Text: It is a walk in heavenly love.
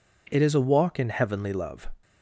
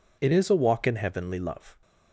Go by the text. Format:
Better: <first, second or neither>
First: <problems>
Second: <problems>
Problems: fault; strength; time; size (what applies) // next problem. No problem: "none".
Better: neither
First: none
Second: none